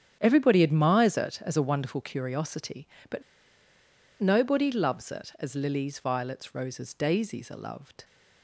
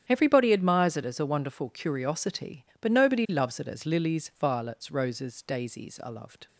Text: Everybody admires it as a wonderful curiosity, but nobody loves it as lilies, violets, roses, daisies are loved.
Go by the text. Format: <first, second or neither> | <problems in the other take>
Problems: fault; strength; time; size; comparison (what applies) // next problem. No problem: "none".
second | starts louder than the rest; strong; until 1.2 s; 9 dB; strong in the second // pauses between "but" and "nobody"; at 3.2 s; 1.0 s long